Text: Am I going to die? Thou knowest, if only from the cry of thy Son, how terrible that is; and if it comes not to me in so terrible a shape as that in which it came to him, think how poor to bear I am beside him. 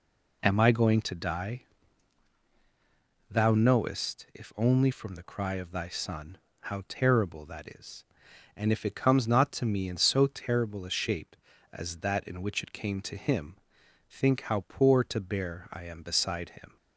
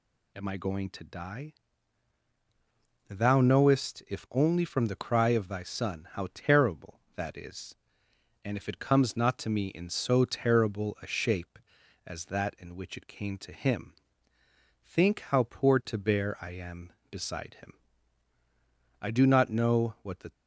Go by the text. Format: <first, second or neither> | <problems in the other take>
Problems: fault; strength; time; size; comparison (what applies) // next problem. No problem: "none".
first | goes on to say "I do not know what the"; from 19.0 s on; 1.3 s long